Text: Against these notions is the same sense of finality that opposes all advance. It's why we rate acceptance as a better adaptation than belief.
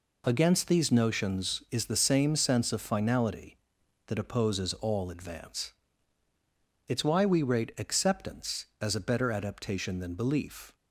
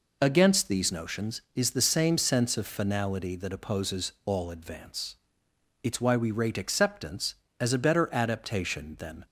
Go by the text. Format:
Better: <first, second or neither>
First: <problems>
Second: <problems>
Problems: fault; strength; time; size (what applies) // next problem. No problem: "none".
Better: first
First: none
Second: stops before "belief"; at 9.2 s